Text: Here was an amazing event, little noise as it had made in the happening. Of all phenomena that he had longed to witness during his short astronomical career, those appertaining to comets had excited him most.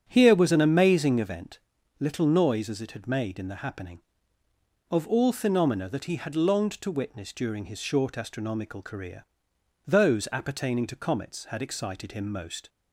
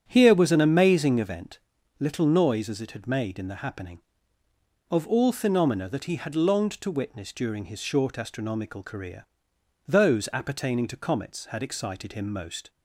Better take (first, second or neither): neither